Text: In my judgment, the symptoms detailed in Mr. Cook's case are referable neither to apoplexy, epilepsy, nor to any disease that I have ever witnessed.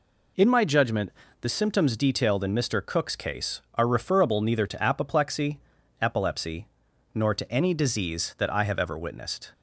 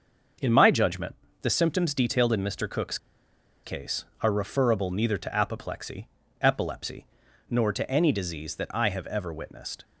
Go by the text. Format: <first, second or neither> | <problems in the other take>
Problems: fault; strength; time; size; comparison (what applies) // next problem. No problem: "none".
first | starts louder than the rest; until 1.6 s; 6.5 dB // pauses between "Cook's" and "case"; noticeable; at 2.9 s; 0.66 s long